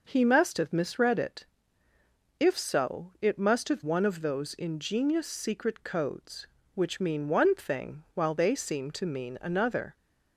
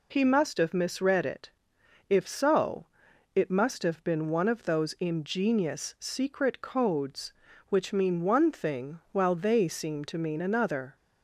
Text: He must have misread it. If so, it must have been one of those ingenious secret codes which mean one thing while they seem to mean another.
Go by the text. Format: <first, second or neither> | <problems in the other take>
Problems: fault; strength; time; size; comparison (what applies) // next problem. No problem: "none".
second | skips "been"; at 3.8 s